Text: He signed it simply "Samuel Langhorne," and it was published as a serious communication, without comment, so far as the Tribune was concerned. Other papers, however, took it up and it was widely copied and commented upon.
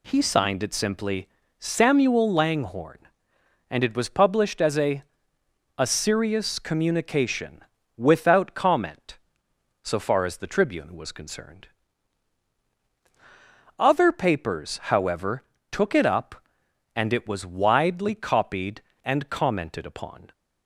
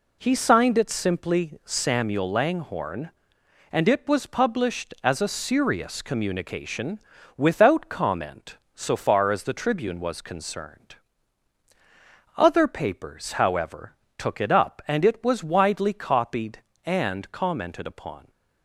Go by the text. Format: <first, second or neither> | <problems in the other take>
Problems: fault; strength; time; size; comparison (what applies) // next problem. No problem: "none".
second | pauses between "simply" and "Samuel"; slight; at 1.2 s; 0.30 s long // says "a" twice; at 5.7 s